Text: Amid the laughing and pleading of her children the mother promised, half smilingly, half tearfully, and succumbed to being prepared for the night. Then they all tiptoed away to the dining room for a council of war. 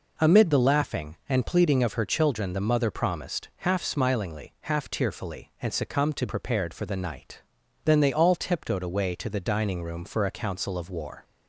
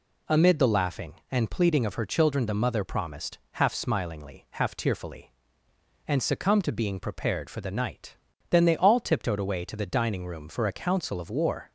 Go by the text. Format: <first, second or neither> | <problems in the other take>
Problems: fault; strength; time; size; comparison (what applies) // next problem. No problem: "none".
second | skips "being"; at 6.2 s